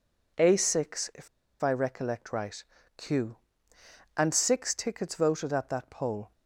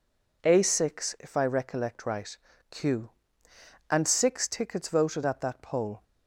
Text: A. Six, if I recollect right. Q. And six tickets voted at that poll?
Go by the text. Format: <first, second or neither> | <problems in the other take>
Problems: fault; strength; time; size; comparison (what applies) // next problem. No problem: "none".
second | pauses between "if" and "I"; slight; at 1.2 s; 0.33 s long